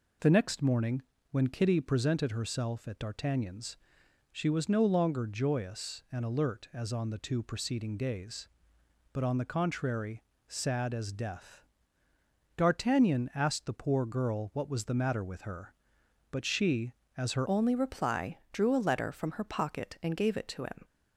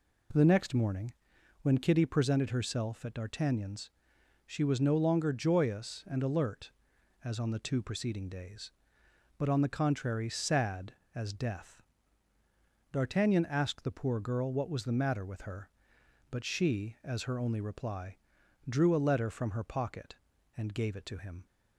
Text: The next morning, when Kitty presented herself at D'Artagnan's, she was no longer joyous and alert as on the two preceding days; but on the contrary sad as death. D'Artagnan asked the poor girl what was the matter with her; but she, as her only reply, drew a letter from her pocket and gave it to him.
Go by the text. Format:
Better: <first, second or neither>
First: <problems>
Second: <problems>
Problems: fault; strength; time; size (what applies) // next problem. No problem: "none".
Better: second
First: pauses between "contrary" and "sad"; slight; at 10.2 s; 0.24 s long // changes voice at "only"; from 17.4 s on; 3.4 s long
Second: none